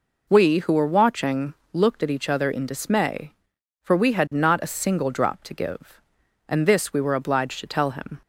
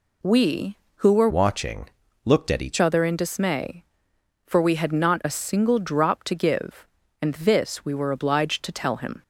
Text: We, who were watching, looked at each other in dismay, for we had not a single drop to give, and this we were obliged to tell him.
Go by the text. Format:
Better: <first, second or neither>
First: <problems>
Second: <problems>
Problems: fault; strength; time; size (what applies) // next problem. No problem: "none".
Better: first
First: none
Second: changes voice from "watching" to "each"; from 1.2 to 2.7 s; 1.5 s long